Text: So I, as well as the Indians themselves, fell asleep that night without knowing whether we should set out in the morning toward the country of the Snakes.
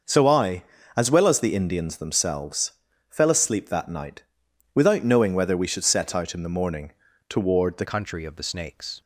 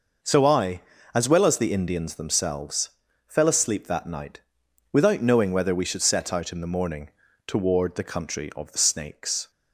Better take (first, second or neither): second